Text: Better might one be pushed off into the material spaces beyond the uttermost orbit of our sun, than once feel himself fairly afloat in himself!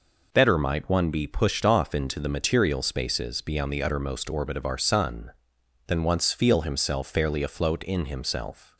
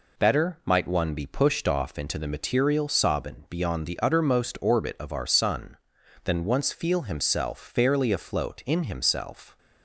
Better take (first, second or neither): first